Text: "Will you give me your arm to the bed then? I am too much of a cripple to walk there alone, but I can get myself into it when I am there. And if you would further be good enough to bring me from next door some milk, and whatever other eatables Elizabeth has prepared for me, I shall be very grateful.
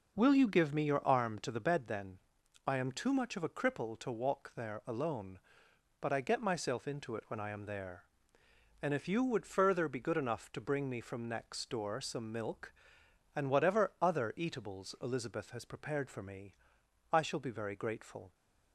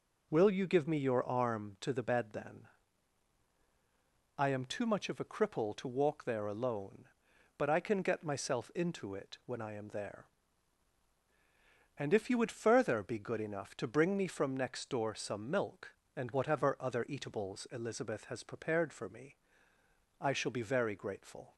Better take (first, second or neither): second